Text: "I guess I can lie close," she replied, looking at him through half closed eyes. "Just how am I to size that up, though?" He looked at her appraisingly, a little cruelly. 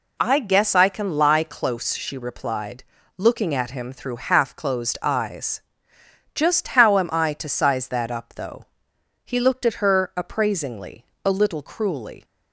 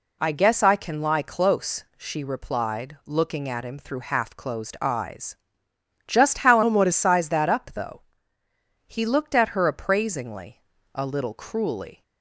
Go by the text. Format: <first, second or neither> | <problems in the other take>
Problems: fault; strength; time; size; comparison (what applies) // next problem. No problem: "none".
first | changes voice from "am" to "to"; from 6.6 to 6.9 s; 0.3 s long